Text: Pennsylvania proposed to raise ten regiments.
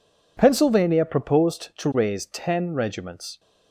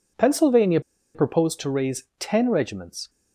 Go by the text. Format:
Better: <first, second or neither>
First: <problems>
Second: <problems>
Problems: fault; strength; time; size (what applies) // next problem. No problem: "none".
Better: first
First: none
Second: pauses between "Pennsylvania" and "proposed"; slight; at 0.7 s; 0.35 s long // pauses between "raise" and "ten"; slight; at 2.0 s; 0.16 s long